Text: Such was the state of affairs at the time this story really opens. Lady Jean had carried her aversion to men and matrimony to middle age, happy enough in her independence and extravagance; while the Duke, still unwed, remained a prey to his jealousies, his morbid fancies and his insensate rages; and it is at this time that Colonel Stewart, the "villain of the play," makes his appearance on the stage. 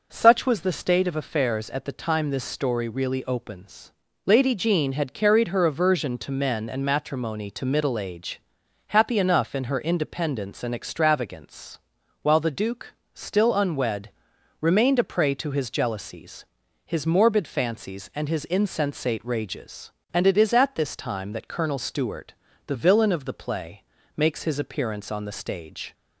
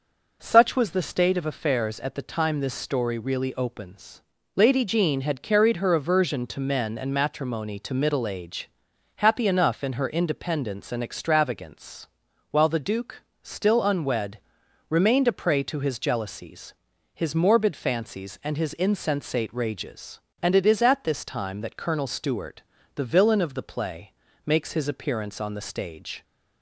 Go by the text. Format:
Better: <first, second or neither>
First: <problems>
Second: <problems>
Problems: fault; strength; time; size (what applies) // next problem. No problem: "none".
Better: neither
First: none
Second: none